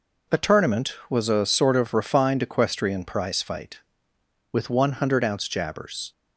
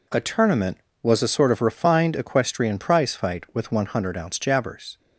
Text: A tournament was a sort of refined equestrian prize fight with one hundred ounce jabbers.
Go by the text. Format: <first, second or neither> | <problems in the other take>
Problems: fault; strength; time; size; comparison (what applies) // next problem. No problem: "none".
neither | none